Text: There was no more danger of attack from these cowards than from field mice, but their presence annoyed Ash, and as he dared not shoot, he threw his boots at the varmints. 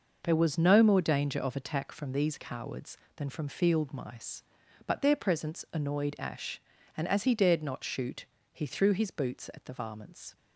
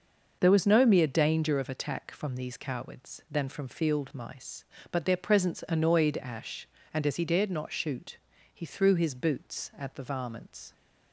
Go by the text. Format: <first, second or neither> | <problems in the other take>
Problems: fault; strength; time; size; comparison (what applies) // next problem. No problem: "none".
first | starts louder than the rest; noticeable; until 1.4 s; 6 dB // says "mere" for "more"; at 0.8 s